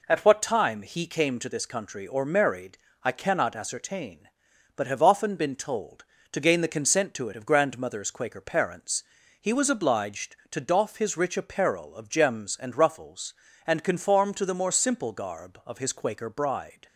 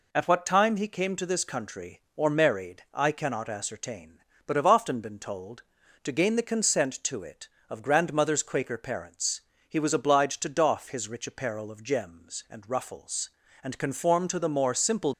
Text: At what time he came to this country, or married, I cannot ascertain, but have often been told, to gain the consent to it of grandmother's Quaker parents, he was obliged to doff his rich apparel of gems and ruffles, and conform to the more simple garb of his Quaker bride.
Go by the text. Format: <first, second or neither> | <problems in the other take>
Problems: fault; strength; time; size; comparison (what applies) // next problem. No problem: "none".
first | stops before "garb of his Quaker bride"; at 15.1 s